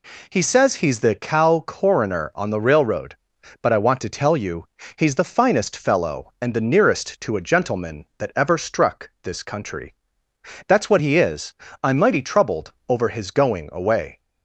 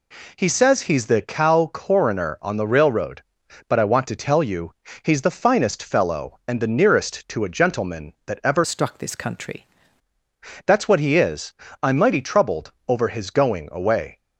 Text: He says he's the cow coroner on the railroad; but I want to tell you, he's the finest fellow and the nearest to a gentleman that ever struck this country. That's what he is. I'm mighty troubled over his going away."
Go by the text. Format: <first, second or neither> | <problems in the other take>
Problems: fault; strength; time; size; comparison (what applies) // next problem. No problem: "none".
first | changes voice from "struck" to "country"; from 8.6 to 9.6 s; 1.0 s long // pauses between "troubled" and "over"; slight; at 12.7 s; 0.16 s long; slight in the first